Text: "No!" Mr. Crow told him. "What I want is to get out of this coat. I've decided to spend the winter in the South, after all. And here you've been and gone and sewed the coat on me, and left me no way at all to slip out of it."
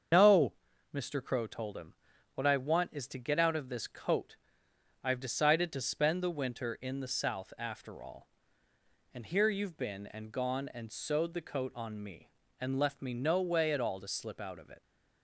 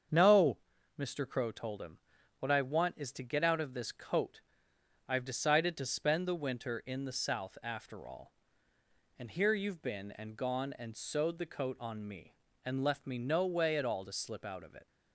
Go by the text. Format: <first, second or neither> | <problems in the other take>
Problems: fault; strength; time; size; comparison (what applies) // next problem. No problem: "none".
second | loses the start of "No"; at 0.1 s; 60 ms // starts louder than the rest; until 1.5 s; 7 dB; strong in the second